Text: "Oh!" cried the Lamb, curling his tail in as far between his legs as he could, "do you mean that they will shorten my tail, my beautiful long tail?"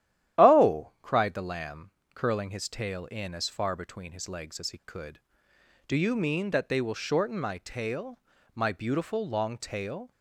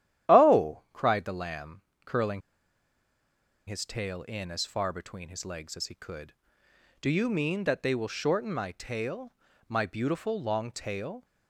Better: first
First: starts louder than the rest; strong; until 1.4 s; 11.5 dB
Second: starts louder than the rest; strong; until 1.3 s; 12 dB // pauses between "curling" and "his"; strong; at 2.4 s; 1.2 s long

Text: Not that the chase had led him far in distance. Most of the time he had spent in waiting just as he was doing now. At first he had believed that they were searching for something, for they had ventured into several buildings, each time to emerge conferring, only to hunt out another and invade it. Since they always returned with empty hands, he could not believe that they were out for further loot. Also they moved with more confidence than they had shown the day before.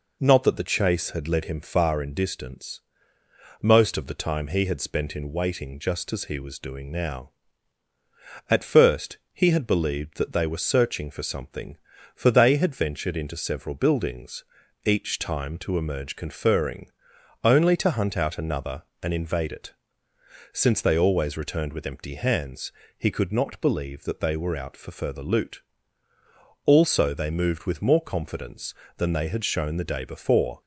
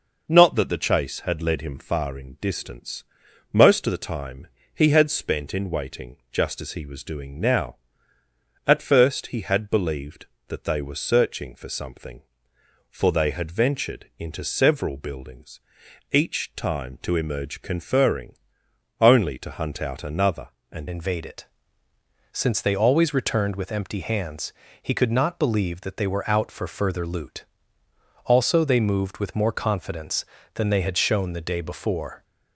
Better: first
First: none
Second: pauses between "time" and "he"; slight; at 4.4 s; 0.26 s long // pauses between "waiting" and "just"; slight; at 6.1 s; 0.16 s long // changes voice at "invade"; from 20.8 s on; 11.4 s long

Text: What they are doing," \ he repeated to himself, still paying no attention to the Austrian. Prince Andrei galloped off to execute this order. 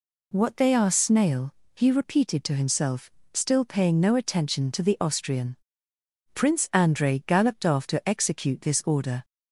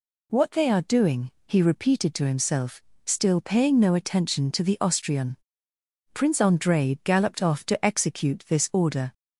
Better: second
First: says "snail" for "doing"; at 0.9 s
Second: none

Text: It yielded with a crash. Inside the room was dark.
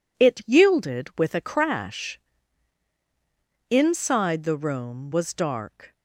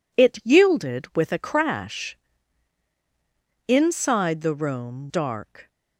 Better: first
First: none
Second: skips "was"; at 5.0 s

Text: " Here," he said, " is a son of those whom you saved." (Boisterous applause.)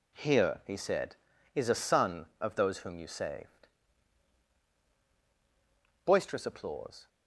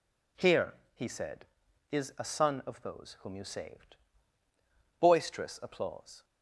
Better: neither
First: none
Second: none

